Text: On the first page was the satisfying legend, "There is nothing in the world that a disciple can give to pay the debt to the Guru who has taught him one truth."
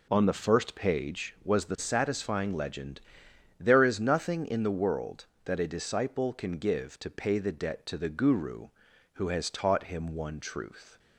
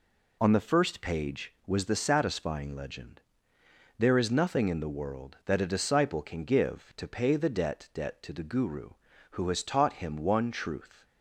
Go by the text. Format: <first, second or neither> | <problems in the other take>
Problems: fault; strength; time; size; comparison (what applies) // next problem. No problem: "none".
first | says "debt" twice; at 7.9 s